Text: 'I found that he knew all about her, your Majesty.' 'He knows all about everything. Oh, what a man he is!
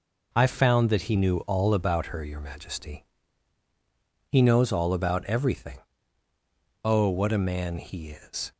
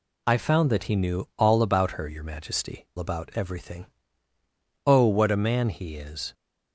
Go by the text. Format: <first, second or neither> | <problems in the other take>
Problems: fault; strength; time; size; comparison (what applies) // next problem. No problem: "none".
first | skips "He knows all"; at 2.9 s